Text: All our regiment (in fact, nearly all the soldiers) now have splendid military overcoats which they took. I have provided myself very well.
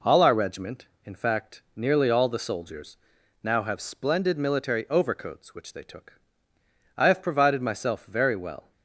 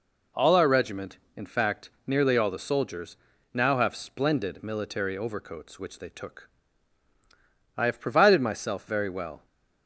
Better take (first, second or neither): neither